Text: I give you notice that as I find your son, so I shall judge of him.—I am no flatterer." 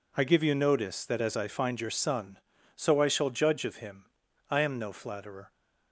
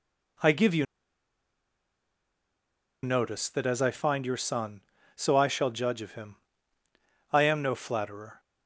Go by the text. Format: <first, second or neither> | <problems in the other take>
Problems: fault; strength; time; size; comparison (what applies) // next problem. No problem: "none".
first | pauses between "you" and "notice"; strong; at 0.8 s; 2.1 s long